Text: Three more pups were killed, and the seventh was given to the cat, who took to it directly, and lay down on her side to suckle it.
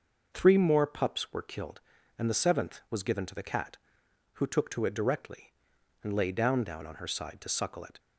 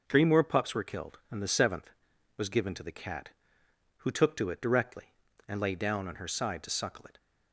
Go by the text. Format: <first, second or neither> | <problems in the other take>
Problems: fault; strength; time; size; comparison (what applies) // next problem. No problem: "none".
second | says "down" twice; at 6.6 s